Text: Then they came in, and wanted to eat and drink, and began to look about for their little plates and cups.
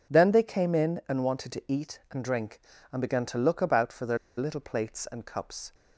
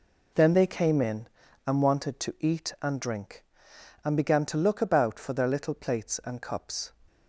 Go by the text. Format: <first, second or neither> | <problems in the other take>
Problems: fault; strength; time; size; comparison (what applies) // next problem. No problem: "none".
second | pauses between "their" and "little"; slight; at 4.1 s; 0.20 s long